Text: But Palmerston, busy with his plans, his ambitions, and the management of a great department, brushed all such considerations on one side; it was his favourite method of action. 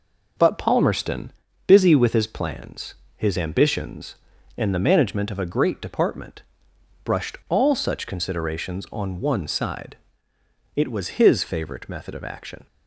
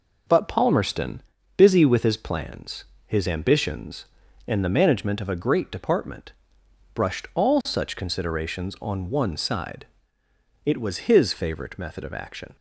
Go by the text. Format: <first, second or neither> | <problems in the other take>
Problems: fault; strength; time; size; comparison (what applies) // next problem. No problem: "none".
neither | none